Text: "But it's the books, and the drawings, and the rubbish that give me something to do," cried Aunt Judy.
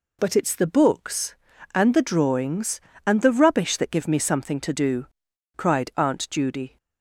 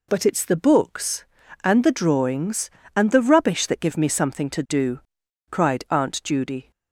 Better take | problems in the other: neither | none

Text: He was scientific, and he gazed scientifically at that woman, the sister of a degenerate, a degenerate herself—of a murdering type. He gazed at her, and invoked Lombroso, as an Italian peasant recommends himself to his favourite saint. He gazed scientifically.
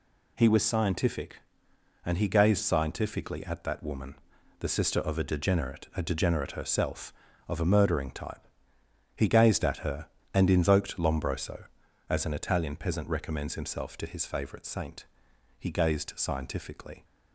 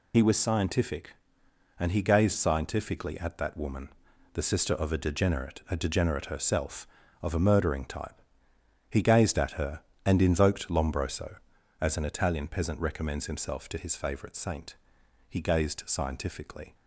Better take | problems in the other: first | loses the start of "He"; at 0.1 s; 50 ms

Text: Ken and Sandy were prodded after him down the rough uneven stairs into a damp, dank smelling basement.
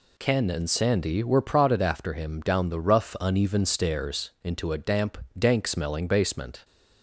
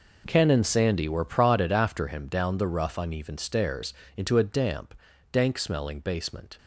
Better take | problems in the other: first | gets quieter; strong; throughout; 14 dB // pauses between "stairs" and "into"; slight; at 3.9 s; 0.24 s long

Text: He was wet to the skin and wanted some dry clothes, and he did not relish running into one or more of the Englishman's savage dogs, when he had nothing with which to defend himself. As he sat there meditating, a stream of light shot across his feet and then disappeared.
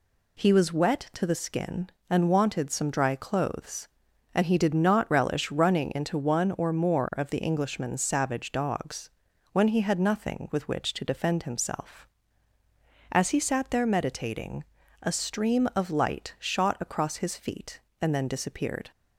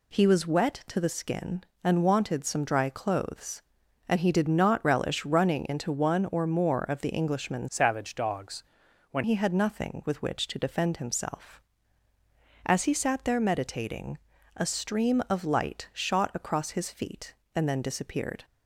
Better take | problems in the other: first | changes voice from "savage" to "when"; from 7.6 to 9.2 s; 1.6 s long

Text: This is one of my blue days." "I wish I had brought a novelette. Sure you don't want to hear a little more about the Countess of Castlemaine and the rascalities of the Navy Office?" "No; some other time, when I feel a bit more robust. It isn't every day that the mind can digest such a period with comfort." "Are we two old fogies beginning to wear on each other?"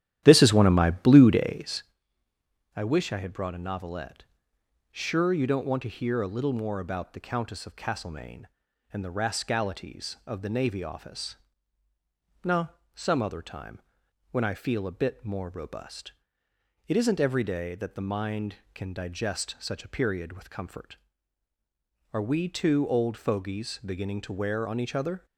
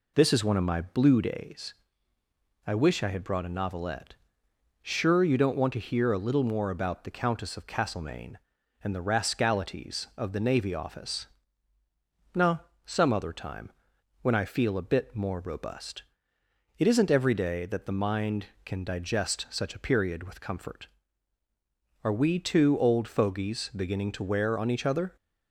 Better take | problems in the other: second | starts louder than the rest; strong; until 1.9 s; 12 dB

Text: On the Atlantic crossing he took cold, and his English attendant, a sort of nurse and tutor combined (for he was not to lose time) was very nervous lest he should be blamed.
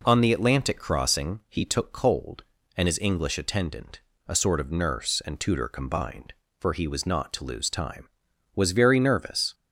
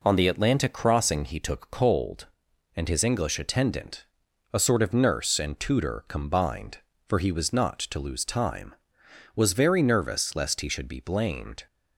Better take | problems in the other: second | stops before "lest he should be blamed"; at 9.5 s

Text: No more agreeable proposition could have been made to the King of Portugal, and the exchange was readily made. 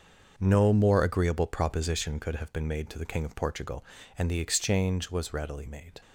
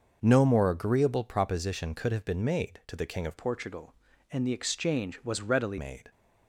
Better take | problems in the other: first | starts louder than the rest; noticeable; until 1.2 s; 6 dB; noticeable in the first // changes voice from "Portugal" to "readily"; from 3.3 to 5.7 s; 2.4 s long

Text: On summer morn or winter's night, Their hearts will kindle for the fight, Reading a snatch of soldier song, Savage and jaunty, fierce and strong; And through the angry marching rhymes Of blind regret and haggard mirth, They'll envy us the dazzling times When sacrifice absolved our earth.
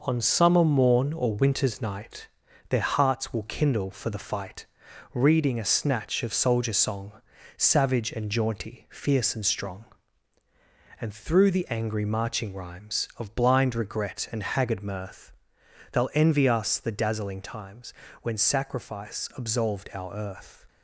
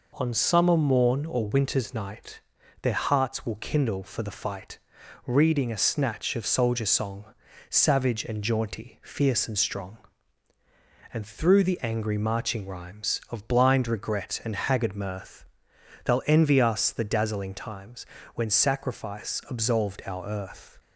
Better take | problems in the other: second | gets quieter; noticeable; throughout; 5.5 dB // pauses between "times" and "When"; slight; at 17.9 s; 0.30 s long; slight in the second

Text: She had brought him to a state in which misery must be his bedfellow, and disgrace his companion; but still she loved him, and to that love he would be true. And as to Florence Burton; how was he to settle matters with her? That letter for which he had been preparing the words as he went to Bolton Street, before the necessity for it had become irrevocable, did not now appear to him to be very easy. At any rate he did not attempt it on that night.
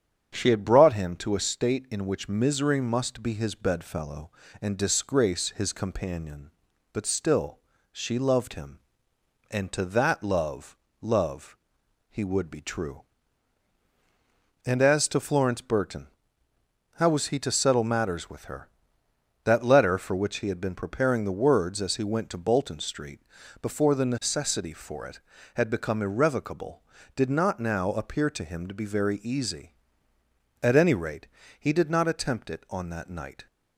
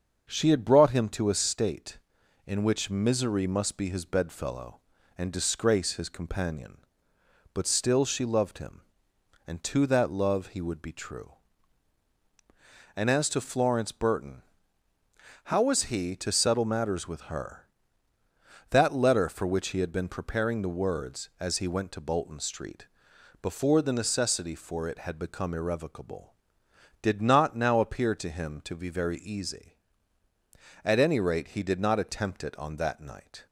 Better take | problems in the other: second | starts louder than the rest; strong; until 1.3 s; 8 dB; also in the second // pauses between "still" and "she"; slight; at 7.5 s; 0.32 s long // says "love" twice; at 11.0 s // pauses between "rate" and "he"; slight; at 31.2 s; 0.34 s long

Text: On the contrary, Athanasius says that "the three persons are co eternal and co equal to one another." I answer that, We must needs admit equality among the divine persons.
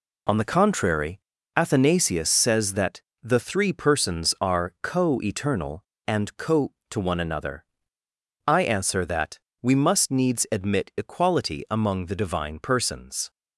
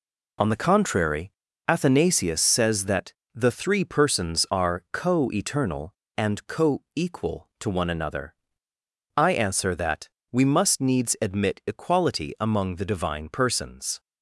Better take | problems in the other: second | pauses between "that" and "the"; slight; at 2.9 s; 0.24 s long; slight in the second // skips "equal"; at 6.8 s

